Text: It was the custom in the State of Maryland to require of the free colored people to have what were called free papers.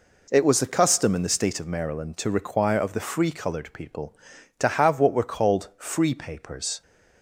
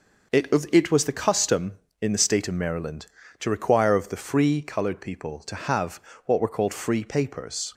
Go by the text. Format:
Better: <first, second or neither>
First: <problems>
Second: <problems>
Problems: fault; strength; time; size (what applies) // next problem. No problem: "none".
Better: first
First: none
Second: says "It" twice; at 0.7 s // pauses between "have" and "what"; slight; at 6.0 s; 0.24 s long